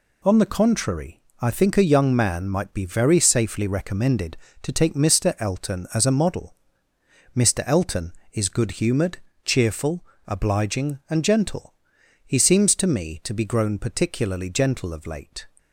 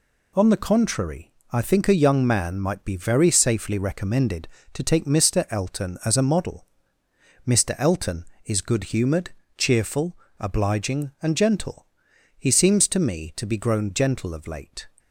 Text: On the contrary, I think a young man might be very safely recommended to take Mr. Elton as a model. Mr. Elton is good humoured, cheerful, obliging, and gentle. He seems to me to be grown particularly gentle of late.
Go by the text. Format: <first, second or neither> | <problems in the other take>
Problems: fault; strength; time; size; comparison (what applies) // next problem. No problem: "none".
first | skips "particularly"; at 13.8 s